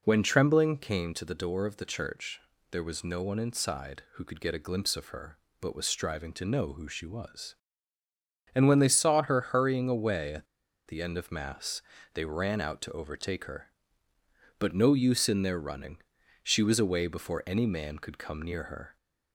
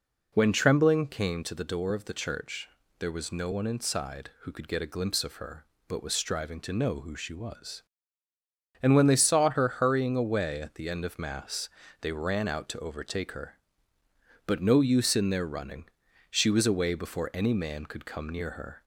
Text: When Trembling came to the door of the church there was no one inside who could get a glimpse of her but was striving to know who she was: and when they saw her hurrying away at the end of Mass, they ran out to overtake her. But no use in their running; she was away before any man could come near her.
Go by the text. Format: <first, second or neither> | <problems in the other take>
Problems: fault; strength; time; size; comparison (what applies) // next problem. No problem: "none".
second | pauses between "church" and "there"; slight; at 2.4 s; 0.30 s long; slight in the second // pauses between "at" and "the"; at 10.4 s; 0.41 s long